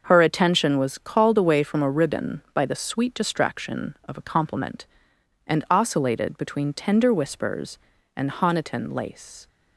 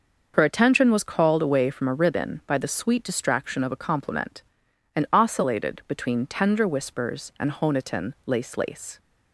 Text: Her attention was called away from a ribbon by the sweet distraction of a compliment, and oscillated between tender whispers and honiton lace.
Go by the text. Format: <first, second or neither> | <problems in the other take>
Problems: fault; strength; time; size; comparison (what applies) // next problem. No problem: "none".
first | starts louder than the rest; until 1.3 s; 6 dB; noticeable in the first // says "lace" twice; at 8.5 s